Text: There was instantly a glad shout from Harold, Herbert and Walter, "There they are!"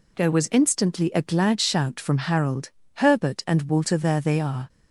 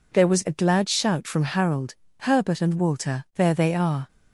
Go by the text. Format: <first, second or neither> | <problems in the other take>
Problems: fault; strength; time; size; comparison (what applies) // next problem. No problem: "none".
first | skips "instantly"; at 0.4 s